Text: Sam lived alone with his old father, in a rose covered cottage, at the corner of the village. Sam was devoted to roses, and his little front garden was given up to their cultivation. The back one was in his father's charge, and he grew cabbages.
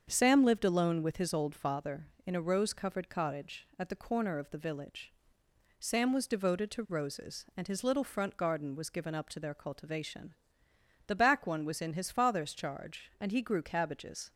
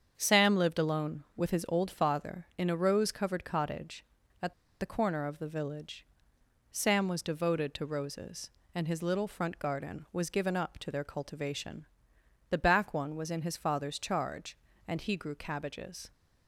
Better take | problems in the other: first | starts louder than the rest; strong; until 1.1 s; 7.5 dB; strong in the first // pauses between "at" and "the"; slight; at 4.5 s; 0.27 s long

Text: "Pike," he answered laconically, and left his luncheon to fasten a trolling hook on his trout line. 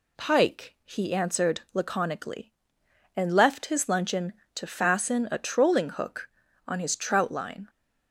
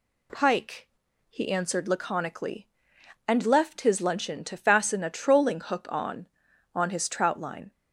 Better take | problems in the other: first | says "on" twice; at 6.7 s

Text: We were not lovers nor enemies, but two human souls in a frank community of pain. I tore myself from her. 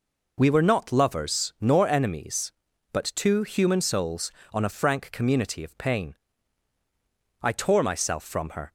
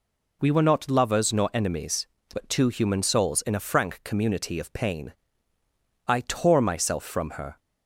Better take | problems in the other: second | says "on" for "in"; at 4.5 s

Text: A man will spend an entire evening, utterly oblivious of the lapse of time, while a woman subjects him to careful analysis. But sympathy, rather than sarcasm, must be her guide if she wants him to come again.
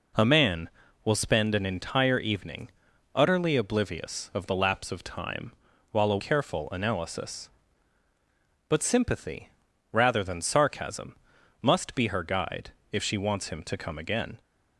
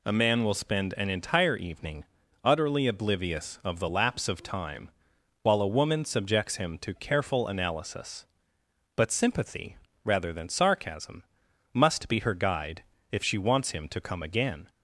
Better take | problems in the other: second | skips "woman subjects him to"; at 6.1 s // pauses between "guide" and "if"; slight; at 12.7 s; 0.20 s long; slight in the second

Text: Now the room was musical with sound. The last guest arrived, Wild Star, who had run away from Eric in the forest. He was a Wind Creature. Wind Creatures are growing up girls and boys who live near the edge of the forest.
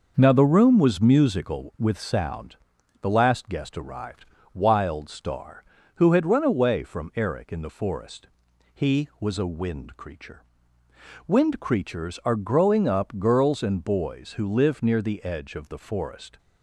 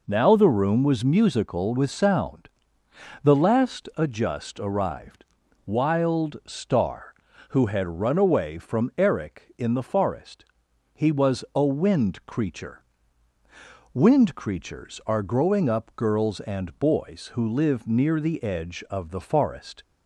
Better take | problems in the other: first | says "adjust" for "guest"; at 3.9 s

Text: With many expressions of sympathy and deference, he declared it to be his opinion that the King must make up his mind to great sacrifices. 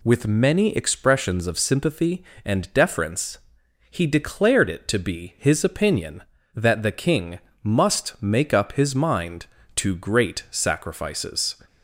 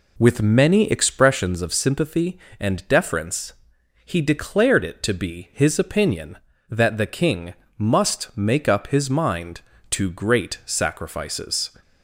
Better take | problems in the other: first | starts louder than the rest; slight; until 1.5 s; 2.5 dB // pauses between "King" and "must"; slight; at 7.5 s; 0.24 s long; slight in the first

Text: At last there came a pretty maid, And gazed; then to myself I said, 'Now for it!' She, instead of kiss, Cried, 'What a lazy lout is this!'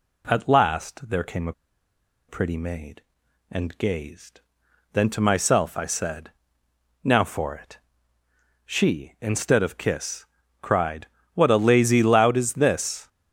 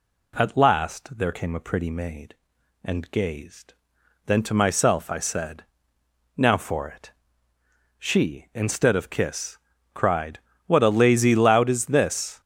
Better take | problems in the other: second | pauses between "a" and "pretty"; noticeable; at 1.5 s; 0.76 s long

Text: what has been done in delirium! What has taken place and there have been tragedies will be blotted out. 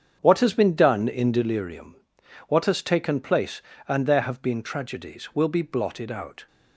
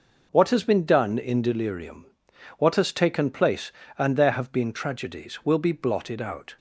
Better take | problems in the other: second | starts louder than the rest; strong; until 1.7 s; 7.5 dB

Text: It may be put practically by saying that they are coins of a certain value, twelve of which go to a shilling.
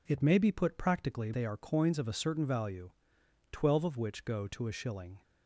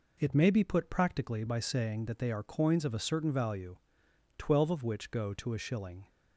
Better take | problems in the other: second | skips "by saying that"; at 1.3 s

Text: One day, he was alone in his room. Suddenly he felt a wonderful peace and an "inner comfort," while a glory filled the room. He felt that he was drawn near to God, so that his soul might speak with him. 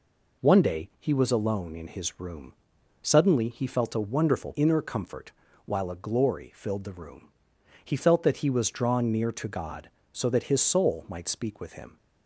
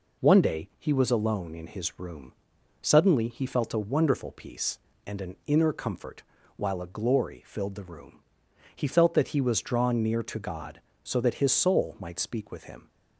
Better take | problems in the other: second | skips "peace and an"; at 4.5 s

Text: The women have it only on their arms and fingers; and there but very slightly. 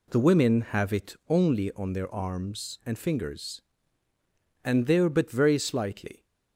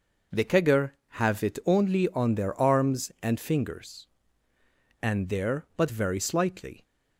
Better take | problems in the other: first | says "kegger" for "women"; at 0.4 s

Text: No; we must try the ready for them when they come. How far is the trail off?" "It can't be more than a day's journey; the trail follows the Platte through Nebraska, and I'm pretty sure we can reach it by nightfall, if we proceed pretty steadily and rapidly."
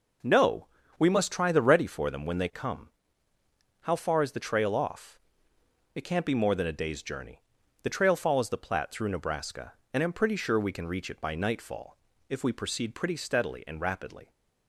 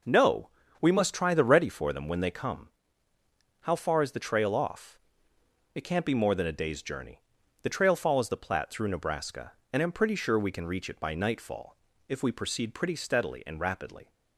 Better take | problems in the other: neither | none

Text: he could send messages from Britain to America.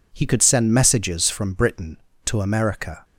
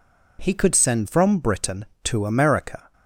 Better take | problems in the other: first | skips "messages"; at 1.0 s

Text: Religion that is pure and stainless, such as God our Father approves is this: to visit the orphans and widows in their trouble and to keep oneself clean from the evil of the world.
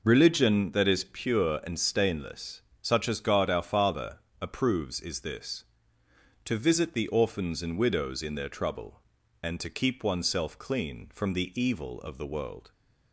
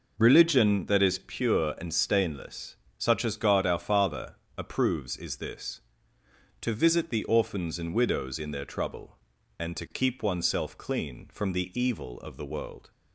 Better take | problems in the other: neither | pauses between "Father" and "approves"; slight; the same in both

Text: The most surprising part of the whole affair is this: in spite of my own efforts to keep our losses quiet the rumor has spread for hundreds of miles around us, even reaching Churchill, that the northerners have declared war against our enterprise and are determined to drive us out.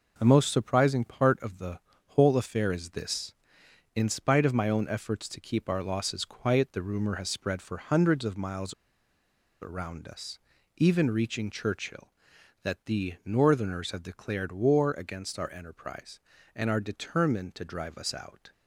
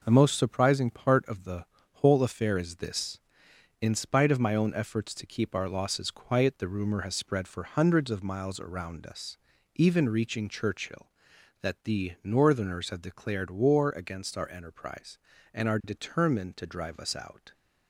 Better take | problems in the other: second | pauses between "the" and "whole"; slight; at 1.7 s; 0.30 s long; slight in the second // pauses between "miles" and "around"; noticeable; at 8.7 s; 0.89 s long

